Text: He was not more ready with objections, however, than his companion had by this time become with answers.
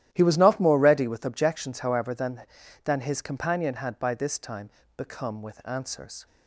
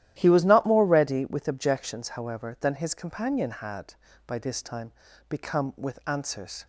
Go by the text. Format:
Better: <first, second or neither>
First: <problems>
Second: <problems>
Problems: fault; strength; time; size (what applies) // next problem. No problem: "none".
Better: second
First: starts louder than the rest; strong; until 1.1 s; 12.5 dB // says "than" twice; at 2.8 s // pauses between "time" and "become"; slight; at 4.6 s; 0.28 s long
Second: starts louder than the rest; strong; until 1.1 s; 12.5 dB // pauses between "time" and "become"; at 4.9 s; 0.38 s long